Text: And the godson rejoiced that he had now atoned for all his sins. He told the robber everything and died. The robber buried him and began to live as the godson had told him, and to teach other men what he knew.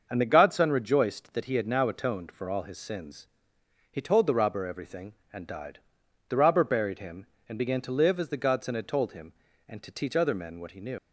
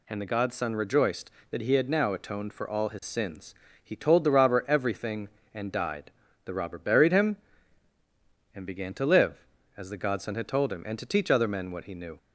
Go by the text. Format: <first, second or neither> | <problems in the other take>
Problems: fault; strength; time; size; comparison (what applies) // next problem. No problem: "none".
second | starts louder than the rest; until 1.1 s; 6.5 dB // leaves "knew" unfinished; at 10.9 s; 105 ms